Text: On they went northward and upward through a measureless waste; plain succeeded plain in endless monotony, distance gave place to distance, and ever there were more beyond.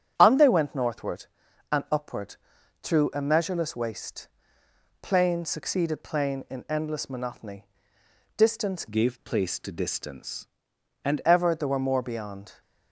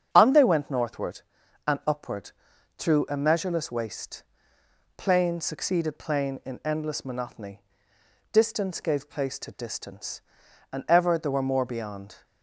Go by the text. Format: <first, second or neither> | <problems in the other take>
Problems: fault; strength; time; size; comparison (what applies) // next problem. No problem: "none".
second | starts louder than the rest; strong; until 1.1 s; 8 dB; strong in the second // pauses between "upward" and "through"; noticeable; at 2.3 s; 0.46 s long; noticeable in the second // changes voice from "gave" to "and"; from 8.8 to 11.2 s; 2.4 s long